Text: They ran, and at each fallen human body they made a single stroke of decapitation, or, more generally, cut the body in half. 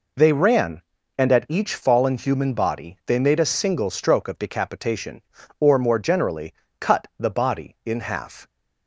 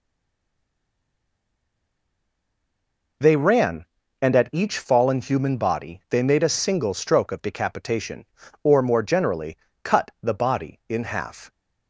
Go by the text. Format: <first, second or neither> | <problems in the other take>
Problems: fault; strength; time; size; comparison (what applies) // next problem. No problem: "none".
first | stays silent before the first word; strong; until 3.2 s; 3.2 s long